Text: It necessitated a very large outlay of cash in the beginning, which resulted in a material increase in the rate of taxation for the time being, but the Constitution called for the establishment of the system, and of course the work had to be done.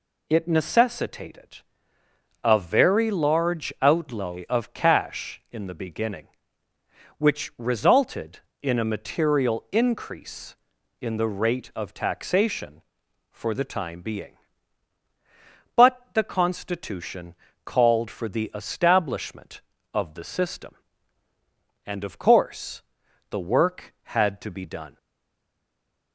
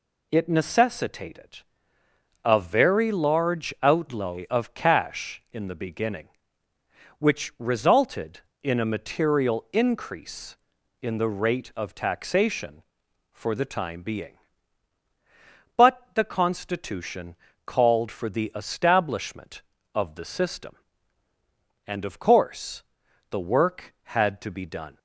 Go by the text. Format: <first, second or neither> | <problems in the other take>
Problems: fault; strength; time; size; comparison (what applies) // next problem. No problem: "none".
second | pauses between "necessitated" and "a"; noticeable; at 1.5 s; 0.86 s long; noticeable in the second // pauses between "Constitution" and "called"; slight; at 17.3 s; 0.32 s long; slight in the second // pauses between "course" and "the"; noticeable; at 22.8 s; 0.48 s long; noticeable in the second // stays silent after the last word; noticeable; from 24.9 s on; 1.2 s long